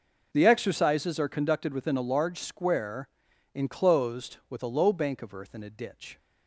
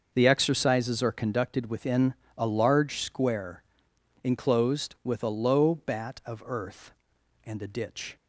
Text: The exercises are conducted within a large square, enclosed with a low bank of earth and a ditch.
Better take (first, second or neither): first